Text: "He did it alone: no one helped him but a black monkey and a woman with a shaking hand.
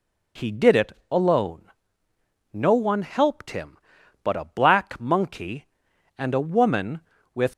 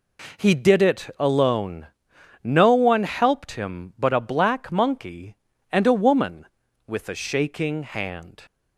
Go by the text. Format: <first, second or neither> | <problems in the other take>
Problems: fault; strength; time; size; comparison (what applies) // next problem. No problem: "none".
second | pauses between "it" and "alone"; slight; at 0.9 s; 0.18 s long // stops before "a shaking hand"; at 7.5 s